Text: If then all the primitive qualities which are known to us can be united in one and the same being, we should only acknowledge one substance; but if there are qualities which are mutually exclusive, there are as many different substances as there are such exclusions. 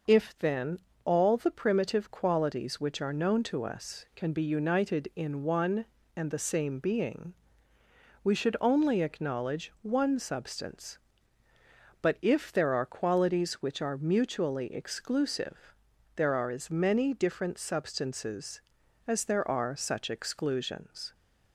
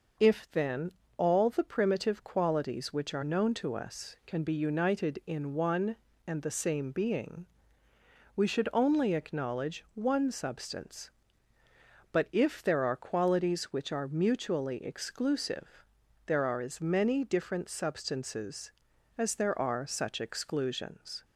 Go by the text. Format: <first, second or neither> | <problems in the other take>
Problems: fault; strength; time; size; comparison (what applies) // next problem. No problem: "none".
neither | pauses between "then" and "all"; slight; the same in both